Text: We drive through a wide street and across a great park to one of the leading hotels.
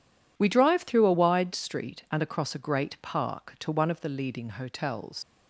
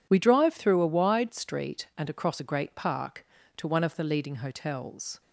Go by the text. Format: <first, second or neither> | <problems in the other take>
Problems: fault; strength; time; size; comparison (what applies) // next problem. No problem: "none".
second | leaves "hotels" unfinished; at 5.2 s; 75 ms